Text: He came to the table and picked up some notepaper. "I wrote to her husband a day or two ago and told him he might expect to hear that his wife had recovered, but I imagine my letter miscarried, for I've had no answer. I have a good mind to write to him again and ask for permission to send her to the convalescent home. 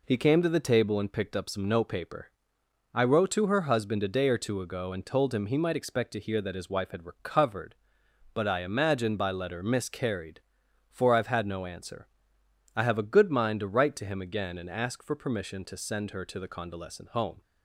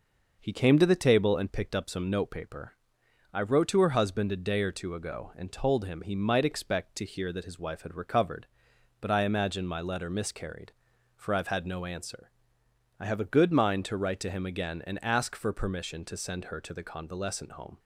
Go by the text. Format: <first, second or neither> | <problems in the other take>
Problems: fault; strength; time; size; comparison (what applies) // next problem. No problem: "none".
second | says "by" for "my"; at 9.1 s